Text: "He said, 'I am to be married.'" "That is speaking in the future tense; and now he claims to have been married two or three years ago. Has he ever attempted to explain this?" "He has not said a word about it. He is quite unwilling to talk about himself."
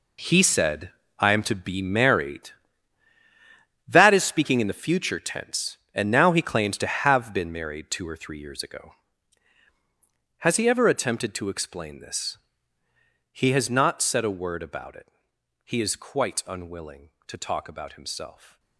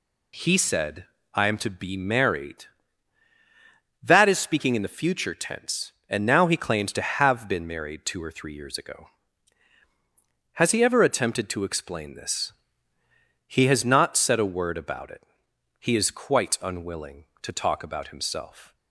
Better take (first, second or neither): second